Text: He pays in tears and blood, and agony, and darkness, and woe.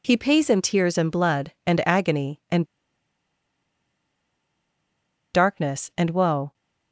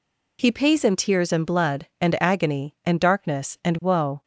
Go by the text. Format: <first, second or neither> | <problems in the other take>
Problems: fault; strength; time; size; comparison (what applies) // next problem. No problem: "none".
second | pauses between "and" and "darkness"; strong; at 2.6 s; 2.7 s long